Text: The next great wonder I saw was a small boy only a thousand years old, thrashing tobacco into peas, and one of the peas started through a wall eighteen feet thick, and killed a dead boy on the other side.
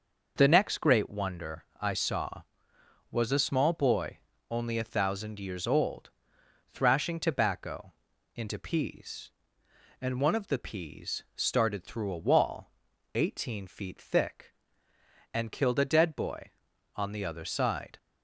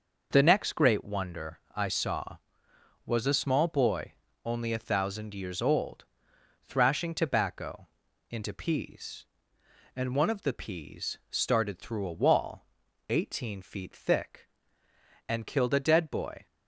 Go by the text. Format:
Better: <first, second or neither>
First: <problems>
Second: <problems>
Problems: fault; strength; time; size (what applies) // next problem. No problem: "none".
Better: first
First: pauses between "wonder" and "I"; slight; at 1.6 s; 0.16 s long // pauses between "boy" and "only"; slight; at 4.1 s; 0.32 s long // pauses between "tobacco" and "into"; at 7.9 s; 0.44 s long // pauses between "wall" and "eighteen"; noticeable; at 12.6 s; 0.46 s long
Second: pauses between "wonder" and "I"; slight; at 1.5 s; 0.16 s long // pauses between "boy" and "only"; slight; at 4.1 s; 0.32 s long // pauses between "tobacco" and "into"; at 7.8 s; 0.44 s long // pauses between "wall" and "eighteen"; noticeable; at 12.6 s; 0.46 s long // stops before "on the other side"; at 16.4 s